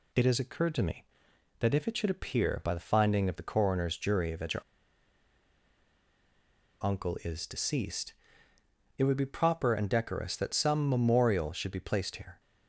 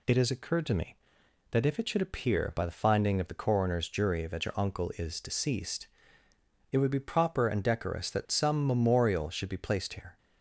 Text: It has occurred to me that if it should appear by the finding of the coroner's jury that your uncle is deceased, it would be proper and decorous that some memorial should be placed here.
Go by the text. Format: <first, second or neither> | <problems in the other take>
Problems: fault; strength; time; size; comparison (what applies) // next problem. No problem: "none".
second | pauses between "your" and "uncle"; strong; at 4.6 s; 2.1 s long